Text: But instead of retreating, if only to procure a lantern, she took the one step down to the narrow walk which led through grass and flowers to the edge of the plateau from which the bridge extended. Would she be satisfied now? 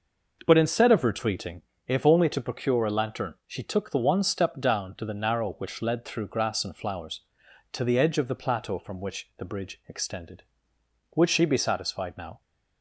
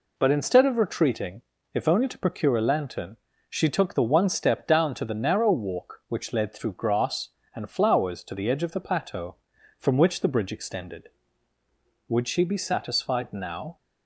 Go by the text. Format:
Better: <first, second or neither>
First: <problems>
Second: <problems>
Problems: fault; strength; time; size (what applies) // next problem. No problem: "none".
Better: second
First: skips "walk"; at 5.5 s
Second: none